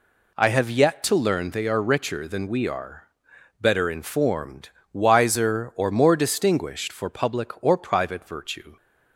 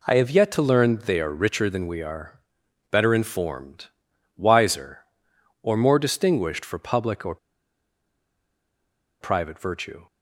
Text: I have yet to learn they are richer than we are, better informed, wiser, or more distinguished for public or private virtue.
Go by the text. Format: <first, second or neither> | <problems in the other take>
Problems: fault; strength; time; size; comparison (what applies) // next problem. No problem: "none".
first | pauses between "or" and "private"; strong; at 7.3 s; 1.8 s long